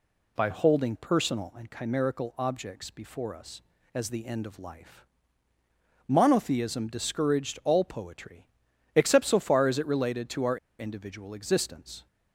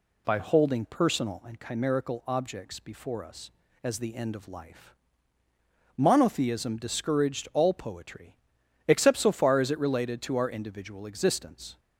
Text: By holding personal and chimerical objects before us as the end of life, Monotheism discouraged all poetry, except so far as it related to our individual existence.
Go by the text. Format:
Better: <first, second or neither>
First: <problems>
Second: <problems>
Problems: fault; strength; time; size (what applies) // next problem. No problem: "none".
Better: second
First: pauses between "our" and "individual"; slight; at 10.5 s; 0.22 s long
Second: none